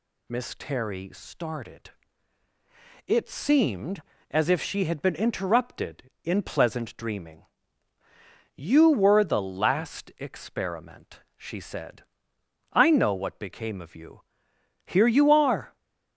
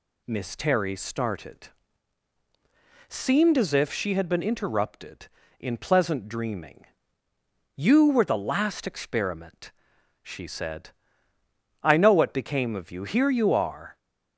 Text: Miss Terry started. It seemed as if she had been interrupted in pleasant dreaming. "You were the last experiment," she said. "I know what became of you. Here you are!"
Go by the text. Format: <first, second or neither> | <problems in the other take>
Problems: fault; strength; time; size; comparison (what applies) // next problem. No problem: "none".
first | skips "It"; at 2.3 s